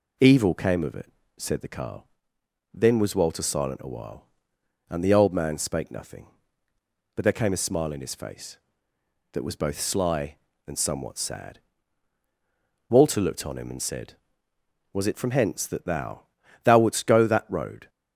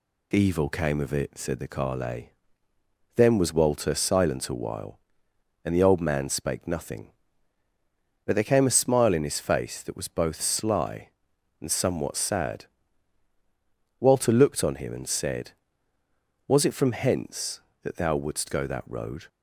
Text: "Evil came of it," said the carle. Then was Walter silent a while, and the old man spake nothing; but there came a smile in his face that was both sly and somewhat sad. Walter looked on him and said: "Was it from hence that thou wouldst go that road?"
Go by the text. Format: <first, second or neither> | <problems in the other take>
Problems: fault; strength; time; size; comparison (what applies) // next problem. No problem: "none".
second | says "thou" twice; at 16.6 s